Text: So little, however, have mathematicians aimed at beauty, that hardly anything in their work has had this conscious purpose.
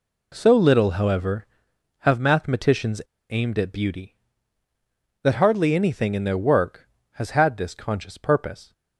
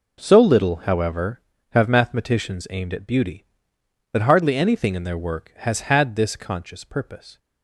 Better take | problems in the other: second | pauses between "mathematicians" and "aimed"; slight; at 3.0 s; 0.26 s long

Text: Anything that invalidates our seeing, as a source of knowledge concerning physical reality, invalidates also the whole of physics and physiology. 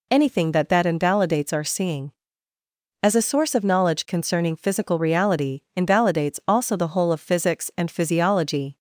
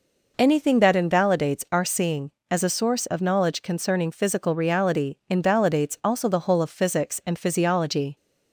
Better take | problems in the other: second | says "that" twice; at 0.6 s

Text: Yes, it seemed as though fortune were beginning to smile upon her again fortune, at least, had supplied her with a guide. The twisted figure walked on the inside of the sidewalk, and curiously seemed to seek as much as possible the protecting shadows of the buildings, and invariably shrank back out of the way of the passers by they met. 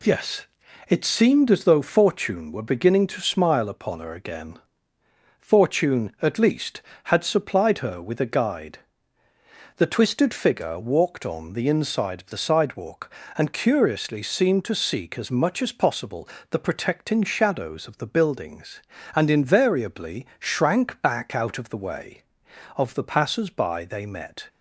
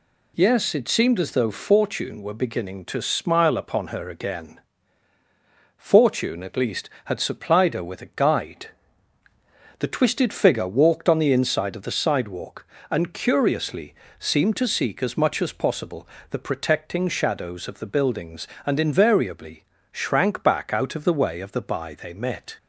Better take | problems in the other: first | pauses between "again" and "fortune"; at 4.5 s; 1.1 s long; noticeable in the first // pauses between "curiously" and "seemed"; slight; at 13.9 s; 0.24 s long // pauses between "possible" and "the"; slight; at 16.0 s; 0.24 s long; slight in the first // pauses between "invariably" and "shrank"; slight; at 19.6 s; 0.28 s long // skips "passers"; at 21.6 s

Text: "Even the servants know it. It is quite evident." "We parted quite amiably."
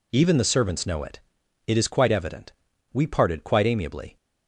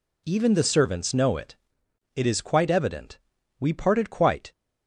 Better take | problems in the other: first | stops before "amiably"; at 4.5 s

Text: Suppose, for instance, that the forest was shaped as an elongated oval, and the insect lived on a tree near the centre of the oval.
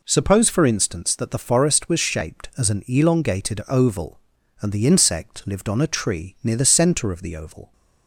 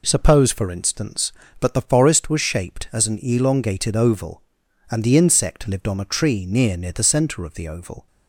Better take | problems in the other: first | says "near" twice; at 6.7 s

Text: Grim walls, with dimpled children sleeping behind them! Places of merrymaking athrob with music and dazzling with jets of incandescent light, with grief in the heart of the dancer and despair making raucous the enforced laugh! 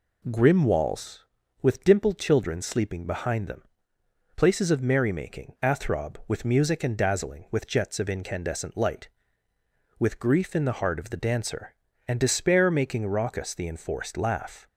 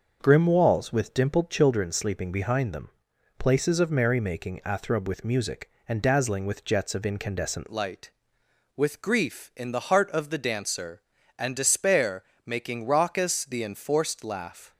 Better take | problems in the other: first | starts louder than the rest; until 1.2 s; 6 dB // changes voice at "light"; from 7.7 s on; 7.0 s long // pauses between "despair" and "making"; slight; at 12.2 s; 0.24 s long

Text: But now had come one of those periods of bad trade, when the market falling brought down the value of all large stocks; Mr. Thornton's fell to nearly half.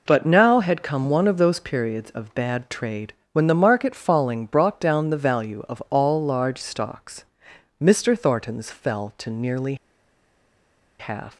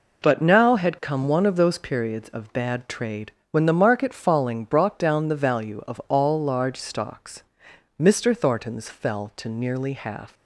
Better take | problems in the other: second | pauses between "nearly" and "half"; strong; at 9.7 s; 1.2 s long

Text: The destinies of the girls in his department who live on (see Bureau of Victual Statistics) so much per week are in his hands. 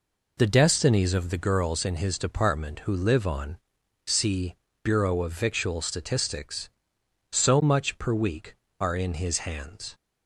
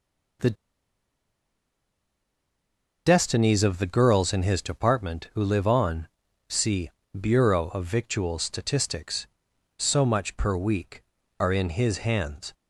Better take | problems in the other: first | pauses between "The" and "destinies"; strong; at 0.5 s; 2.5 s long // pauses between "see" and "Bureau"; slight; at 6.9 s; 0.26 s long; slight in the first

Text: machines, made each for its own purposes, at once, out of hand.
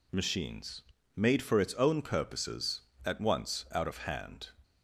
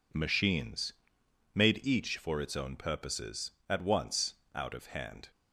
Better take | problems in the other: second | skips "each"; at 1.4 s

